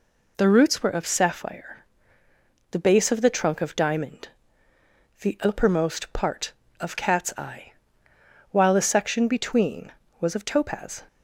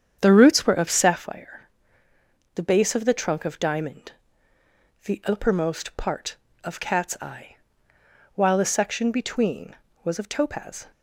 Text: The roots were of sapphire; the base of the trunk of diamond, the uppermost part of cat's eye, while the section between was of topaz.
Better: first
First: none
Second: starts louder than the rest; strong; until 1.2 s; 8 dB

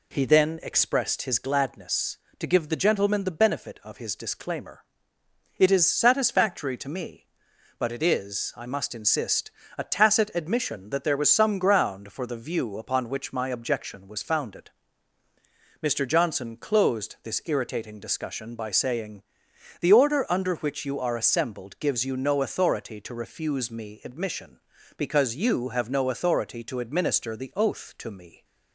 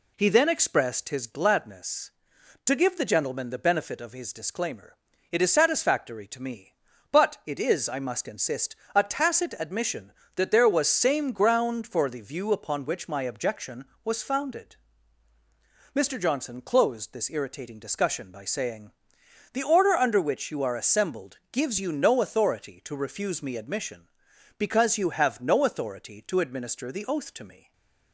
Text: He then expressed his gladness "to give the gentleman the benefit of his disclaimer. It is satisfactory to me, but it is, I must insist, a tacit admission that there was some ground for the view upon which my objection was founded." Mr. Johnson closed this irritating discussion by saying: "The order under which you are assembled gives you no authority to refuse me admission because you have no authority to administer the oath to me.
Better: first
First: none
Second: says "same" for "some"; at 10.8 s // stays silent after the last word; slight; from 27.5 s on; 0.6 s long

